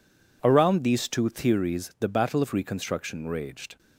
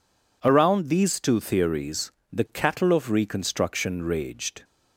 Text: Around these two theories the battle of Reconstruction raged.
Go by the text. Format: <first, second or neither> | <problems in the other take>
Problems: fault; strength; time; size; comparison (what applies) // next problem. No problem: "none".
first | pauses between "theories" and "the"; slight; at 2.1 s; 0.18 s long // says "cattle" for "battle"; at 2.4 s